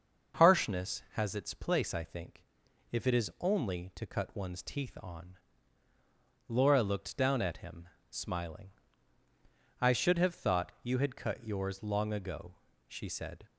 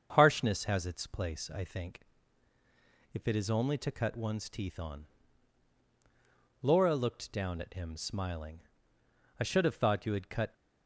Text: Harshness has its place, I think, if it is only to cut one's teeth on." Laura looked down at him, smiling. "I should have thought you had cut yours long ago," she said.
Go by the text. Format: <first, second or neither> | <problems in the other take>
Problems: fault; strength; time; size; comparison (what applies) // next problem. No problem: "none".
first | starts louder than the rest; until 1.1 s; 7 dB; also in the first // stops before "yours long ago she said"; at 10.5 s